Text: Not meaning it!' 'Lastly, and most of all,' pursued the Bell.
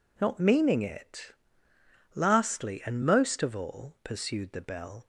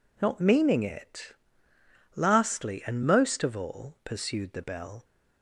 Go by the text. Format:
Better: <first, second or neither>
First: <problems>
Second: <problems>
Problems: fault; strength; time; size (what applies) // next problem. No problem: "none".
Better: neither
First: none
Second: none